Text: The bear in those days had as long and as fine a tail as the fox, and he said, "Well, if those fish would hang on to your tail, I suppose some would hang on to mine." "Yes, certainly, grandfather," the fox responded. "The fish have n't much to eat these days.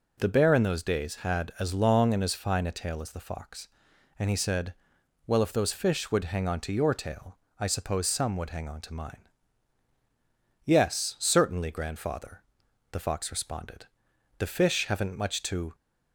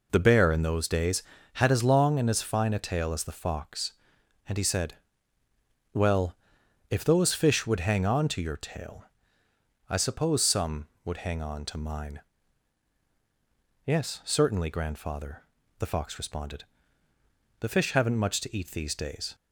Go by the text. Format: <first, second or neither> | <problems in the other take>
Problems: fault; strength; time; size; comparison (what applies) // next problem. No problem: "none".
second | stops before "eat these days"; at 15.7 s